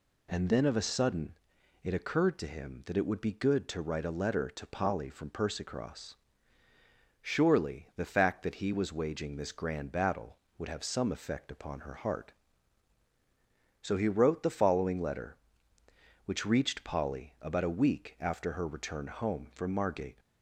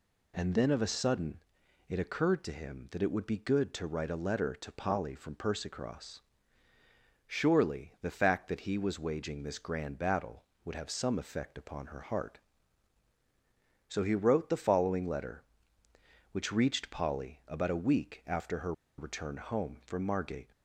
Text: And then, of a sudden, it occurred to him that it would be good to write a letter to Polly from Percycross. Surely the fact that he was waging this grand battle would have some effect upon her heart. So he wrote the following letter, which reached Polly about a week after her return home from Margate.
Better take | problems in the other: first | pauses between "her" and "return"; slight; at 18.7 s; 0.25 s long

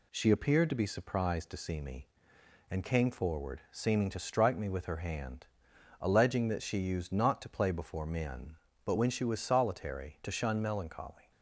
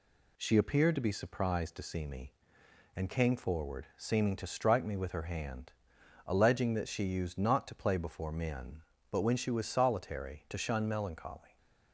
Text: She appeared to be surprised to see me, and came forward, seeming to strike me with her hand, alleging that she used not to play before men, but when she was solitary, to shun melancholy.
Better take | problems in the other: neither | none

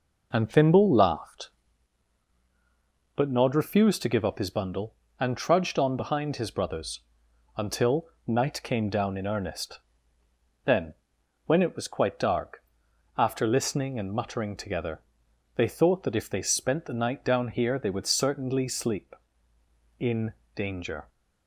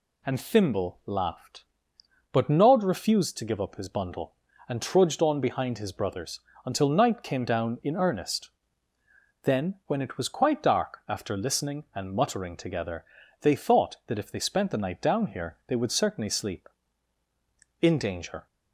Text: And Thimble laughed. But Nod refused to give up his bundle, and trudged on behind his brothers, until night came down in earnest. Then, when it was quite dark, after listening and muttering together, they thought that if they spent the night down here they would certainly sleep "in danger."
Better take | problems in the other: second | starts louder than the rest; noticeable; until 1.7 s; 5 dB // pauses between "until" and "night"; slight; at 8.0 s; 0.20 s long // pauses between "in" and "danger"; slight; at 20.3 s; 0.20 s long

